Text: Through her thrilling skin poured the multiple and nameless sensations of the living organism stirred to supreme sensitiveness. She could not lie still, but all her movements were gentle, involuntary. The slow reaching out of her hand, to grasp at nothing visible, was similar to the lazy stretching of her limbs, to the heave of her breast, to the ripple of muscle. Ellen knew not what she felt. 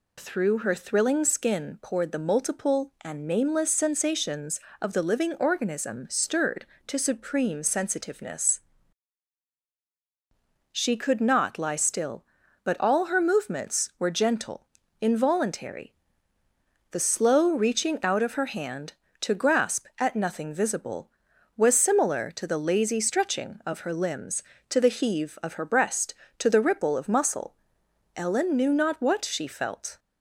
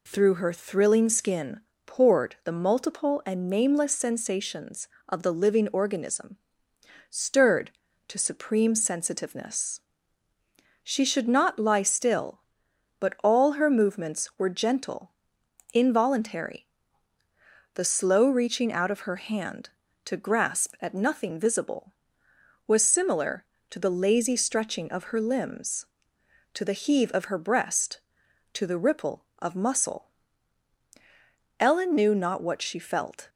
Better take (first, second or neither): first